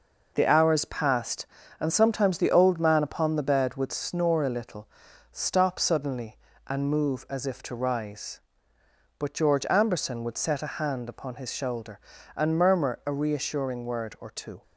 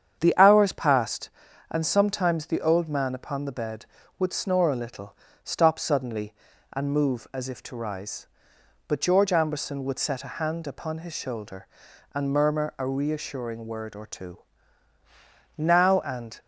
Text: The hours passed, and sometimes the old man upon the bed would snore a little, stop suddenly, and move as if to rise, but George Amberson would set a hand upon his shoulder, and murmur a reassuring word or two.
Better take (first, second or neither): first